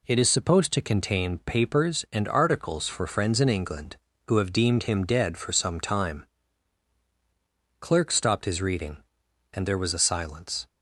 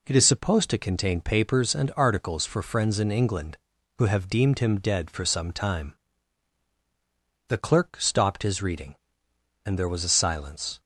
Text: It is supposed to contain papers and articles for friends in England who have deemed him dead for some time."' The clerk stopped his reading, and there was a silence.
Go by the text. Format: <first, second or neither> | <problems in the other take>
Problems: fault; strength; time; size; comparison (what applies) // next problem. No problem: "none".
second | skips "The"; at 7.0 s